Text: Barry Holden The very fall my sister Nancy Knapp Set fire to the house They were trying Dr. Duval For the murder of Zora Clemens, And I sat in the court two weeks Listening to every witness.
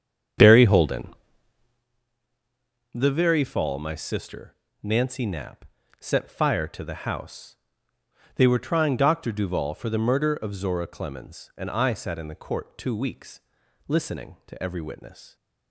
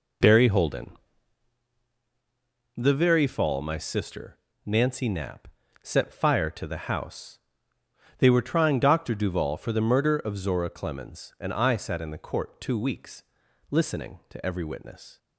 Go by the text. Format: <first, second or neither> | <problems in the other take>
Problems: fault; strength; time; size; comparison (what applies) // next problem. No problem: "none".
second | starts louder than the rest; strong; until 1.9 s; 8 dB // pauses between "Holden" and "The"; strong; at 1.1 s; 1.8 s long; strong in the second // pauses between "sister" and "Nancy"; slight; at 4.5 s; 0.26 s long; slight in the second // pauses between "Knapp" and "Set"; slight; at 5.6 s; 0.34 s long; slight in the second // pauses between "house" and "They"; noticeable; at 7.5 s; 0.78 s long; noticeable in the second // pauses between "weeks" and "Listening"; noticeable; at 13.4 s; 0.48 s long; noticeable in the second